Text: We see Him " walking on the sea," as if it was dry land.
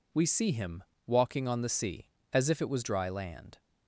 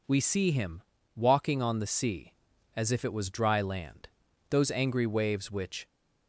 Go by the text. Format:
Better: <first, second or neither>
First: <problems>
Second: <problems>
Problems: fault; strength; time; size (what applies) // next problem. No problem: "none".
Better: first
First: none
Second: goes on to say "Those angry waves which"; from 4.4 s on; 1.3 s long